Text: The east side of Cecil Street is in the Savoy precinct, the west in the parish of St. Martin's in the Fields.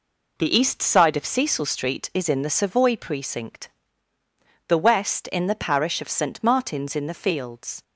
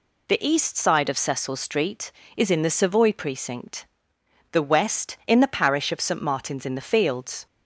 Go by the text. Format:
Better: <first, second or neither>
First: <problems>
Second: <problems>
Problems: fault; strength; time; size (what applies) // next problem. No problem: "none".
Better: neither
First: none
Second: none